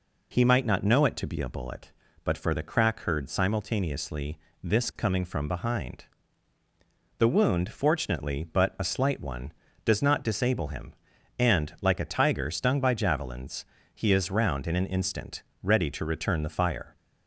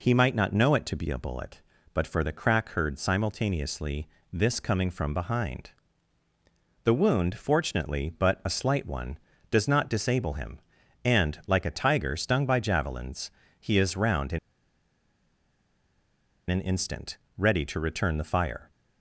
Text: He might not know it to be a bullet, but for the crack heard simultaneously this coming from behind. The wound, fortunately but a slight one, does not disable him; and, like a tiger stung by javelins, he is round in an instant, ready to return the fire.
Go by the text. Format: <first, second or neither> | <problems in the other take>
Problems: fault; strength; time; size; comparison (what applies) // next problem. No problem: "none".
first | pauses between "simultaneously" and "this"; slight; at 4.0 s; 0.26 s long; slight in the first // pauses between "in" and "an"; strong; at 14.3 s; 2.1 s long